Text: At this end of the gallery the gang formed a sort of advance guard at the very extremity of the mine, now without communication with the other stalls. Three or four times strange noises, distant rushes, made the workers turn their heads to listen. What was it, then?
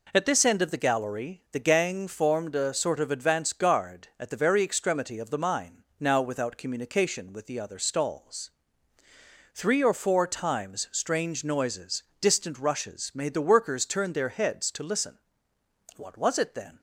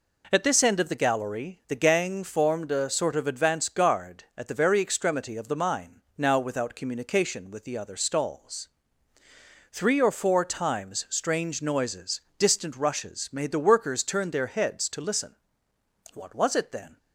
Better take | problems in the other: neither | none

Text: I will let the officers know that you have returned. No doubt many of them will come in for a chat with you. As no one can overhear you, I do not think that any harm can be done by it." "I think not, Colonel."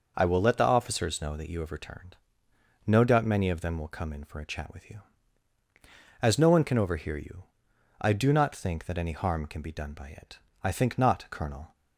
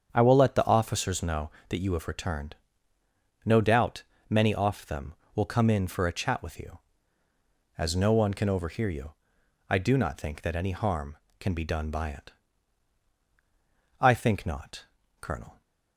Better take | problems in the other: first | starts louder than the rest; strong; until 1.1 s; 7.5 dB // pauses between "doubt" and "many"; slight; at 4.0 s; 0.26 s long // says "off" for "of"; at 4.5 s

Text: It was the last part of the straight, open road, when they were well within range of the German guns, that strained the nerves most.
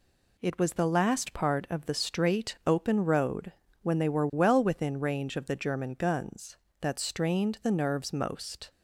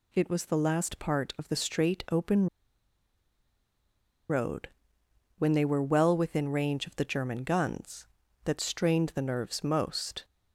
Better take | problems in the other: first | pauses between "open" and "road"; strong; at 2.4 s; 1.8 s long

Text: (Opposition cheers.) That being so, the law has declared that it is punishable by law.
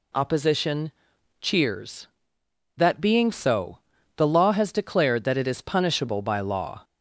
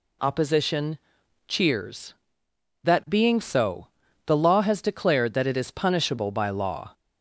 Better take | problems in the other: neither | pauses between "Opposition" and "cheers"; noticeable; the same in both

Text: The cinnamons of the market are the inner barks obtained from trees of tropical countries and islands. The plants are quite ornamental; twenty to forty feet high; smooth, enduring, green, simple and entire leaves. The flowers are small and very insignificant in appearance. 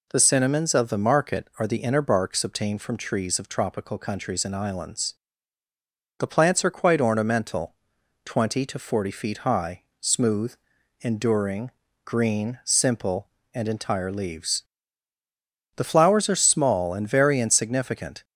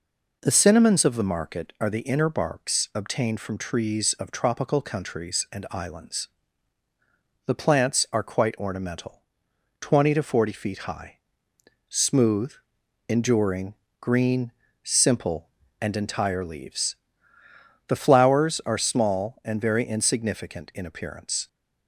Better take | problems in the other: second | stops before "in appearance"; at 18.2 s

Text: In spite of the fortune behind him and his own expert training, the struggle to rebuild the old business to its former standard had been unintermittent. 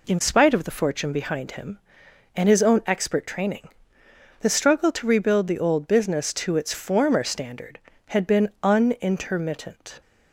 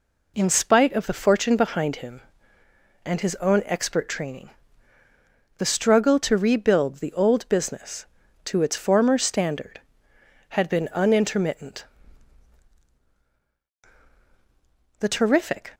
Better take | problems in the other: first | goes on to say "The terrific"; noticeable; from 14.9 s on; 0.72 s long

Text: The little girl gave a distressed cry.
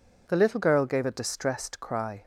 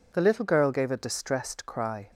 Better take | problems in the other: neither | none

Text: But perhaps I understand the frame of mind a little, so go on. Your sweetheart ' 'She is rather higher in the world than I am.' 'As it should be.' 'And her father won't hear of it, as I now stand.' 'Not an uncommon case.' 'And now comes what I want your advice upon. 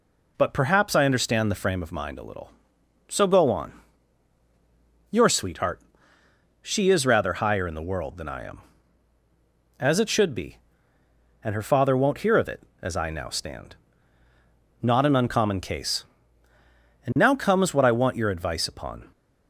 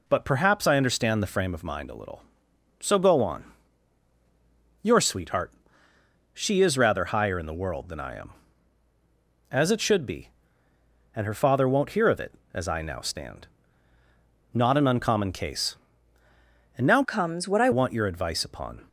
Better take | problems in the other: first | changes voice from "comes" to "I"; from 17.0 to 17.7 s; 0.7 s long

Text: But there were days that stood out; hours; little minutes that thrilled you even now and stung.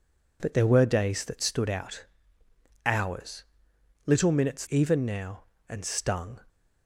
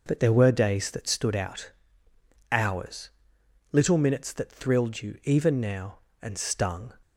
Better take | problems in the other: second | skips "that thrilled you"; at 4.6 s

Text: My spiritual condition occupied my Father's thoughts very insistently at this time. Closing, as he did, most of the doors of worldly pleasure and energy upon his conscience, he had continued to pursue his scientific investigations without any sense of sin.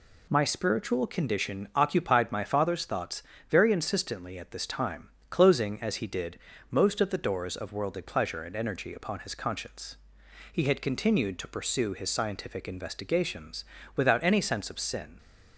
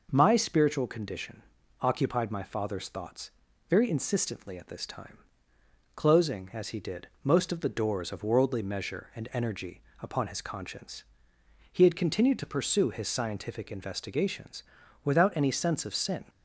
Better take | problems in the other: first | pauses between "condition" and "occupied"; at 1.4 s; 0.38 s long // pauses between "thoughts" and "very"; at 3.2 s; 0.38 s long; slight in the first // says "measure" for "pleasure"; at 8.6 s // pauses between "energy" and "upon"; slight; at 9.8 s; 0.20 s long // pauses between "investigations" and "without"; at 14.6 s; 0.40 s long; slight in the first

